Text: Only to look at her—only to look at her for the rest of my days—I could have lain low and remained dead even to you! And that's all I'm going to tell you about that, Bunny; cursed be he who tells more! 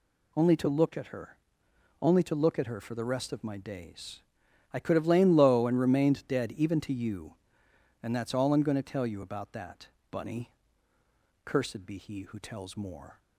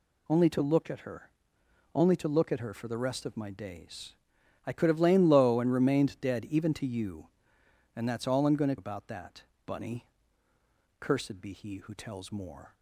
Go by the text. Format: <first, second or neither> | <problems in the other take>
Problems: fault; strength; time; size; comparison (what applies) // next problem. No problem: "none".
first | skips "tell you"; at 8.7 s